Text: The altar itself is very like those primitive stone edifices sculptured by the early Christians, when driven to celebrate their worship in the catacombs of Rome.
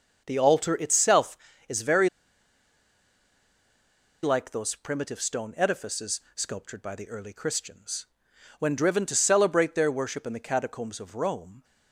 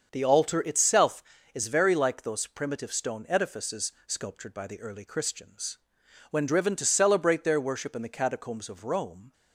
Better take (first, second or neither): second